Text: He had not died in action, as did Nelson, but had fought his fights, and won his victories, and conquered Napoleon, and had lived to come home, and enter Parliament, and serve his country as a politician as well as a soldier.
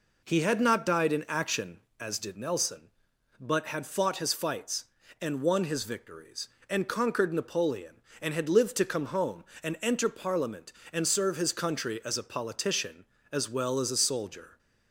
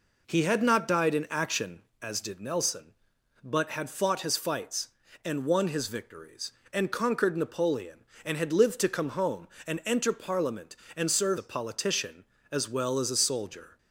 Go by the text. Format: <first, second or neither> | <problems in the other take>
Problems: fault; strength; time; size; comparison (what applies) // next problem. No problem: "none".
first | skips "his country as"; at 11.3 s